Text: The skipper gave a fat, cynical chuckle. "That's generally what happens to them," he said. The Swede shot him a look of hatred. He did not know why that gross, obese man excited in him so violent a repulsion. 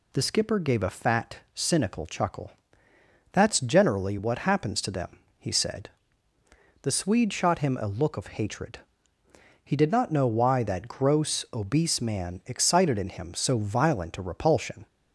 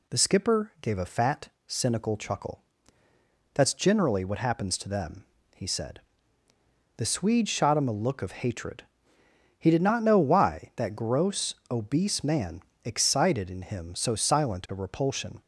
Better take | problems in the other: first | pauses between "man" and "excited"; slight; at 12.6 s; 0.22 s long // says "silent" for "violent"; at 14.1 s

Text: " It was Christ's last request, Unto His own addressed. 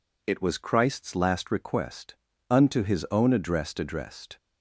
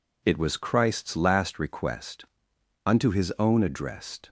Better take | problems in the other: second | says "addressed" twice; at 3.7 s

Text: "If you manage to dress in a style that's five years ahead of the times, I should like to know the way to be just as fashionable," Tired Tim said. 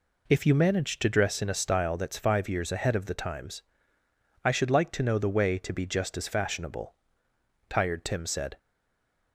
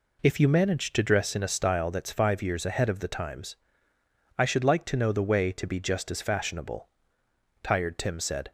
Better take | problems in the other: second | stays silent after the last word; slight; from 8.5 s on; 0.8 s long

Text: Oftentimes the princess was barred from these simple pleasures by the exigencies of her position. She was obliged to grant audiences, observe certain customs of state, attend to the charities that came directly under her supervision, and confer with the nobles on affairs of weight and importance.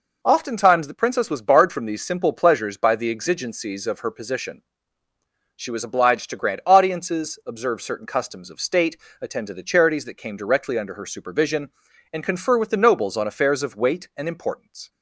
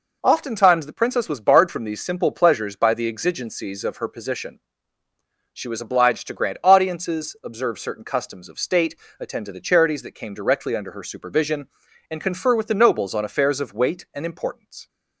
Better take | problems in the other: neither | none

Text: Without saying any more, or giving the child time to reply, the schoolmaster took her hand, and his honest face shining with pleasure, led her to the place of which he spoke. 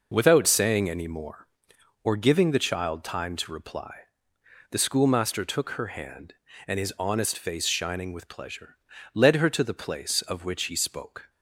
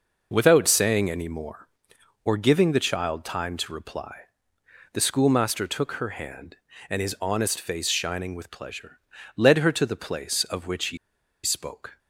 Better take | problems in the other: first | pauses between "he" and "spoke"; noticeable; at 10.9 s; 0.47 s long

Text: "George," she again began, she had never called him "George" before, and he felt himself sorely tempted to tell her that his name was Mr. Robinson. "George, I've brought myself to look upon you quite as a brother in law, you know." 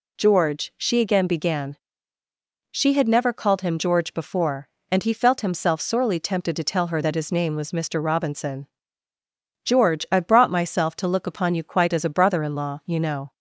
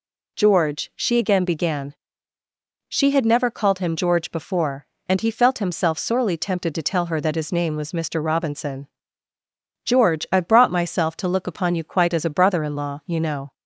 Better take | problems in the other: neither | none

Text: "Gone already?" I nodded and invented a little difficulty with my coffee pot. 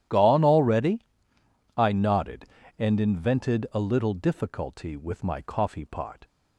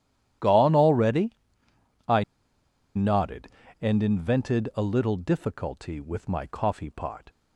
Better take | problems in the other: first | pauses between "I" and "nodded"; noticeable; at 2.2 s; 0.72 s long

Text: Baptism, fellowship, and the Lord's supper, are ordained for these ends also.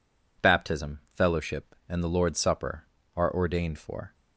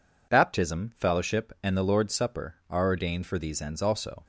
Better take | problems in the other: second | stops before "these ends also"; at 4.1 s

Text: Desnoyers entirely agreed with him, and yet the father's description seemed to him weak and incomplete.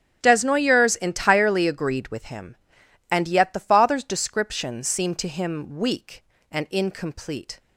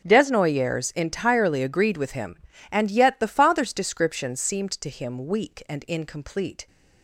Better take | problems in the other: neither | starts louder than the rest; the same in both

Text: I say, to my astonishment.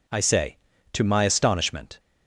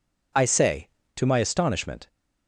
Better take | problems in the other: neither | none

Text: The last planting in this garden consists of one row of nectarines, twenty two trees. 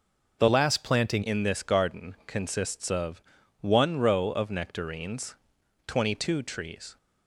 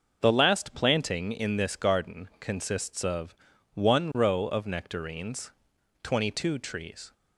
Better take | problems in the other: second | changes voice from "last" to "planting"; from 0.4 to 1.2 s; 0.8 s long // pauses between "of" and "one"; at 3.2 s; 0.40 s long; also in the second

